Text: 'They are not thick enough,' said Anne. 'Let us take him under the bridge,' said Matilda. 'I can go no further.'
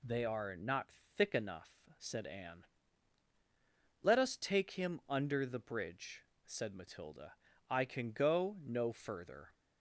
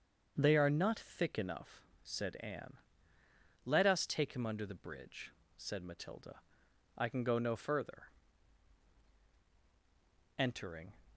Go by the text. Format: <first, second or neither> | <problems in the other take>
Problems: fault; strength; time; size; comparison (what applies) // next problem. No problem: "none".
first | starts louder than the rest; until 1.3 s; 7 dB // goes on to say "Entering"; from 10.3 s on; 0.60 s long